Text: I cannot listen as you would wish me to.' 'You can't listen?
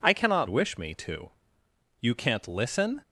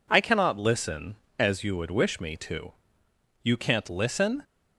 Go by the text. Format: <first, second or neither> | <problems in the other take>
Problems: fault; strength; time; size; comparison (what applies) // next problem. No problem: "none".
second | skips "listen as you would"; at 0.4 s